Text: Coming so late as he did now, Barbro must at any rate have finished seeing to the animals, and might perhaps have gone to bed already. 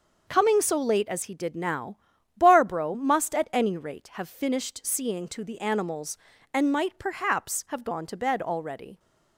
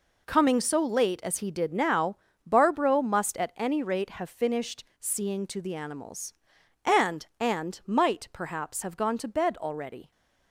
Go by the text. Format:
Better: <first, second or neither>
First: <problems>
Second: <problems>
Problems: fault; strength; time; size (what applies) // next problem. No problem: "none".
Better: first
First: none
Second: says "and" twice; at 7.4 s